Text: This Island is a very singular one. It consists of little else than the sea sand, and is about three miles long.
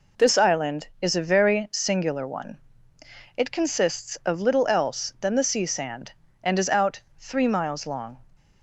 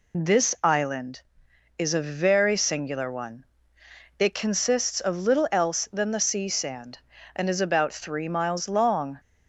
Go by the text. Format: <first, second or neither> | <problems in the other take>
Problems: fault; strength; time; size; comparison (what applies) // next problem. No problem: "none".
second | says "out" for "about"; at 6.6 s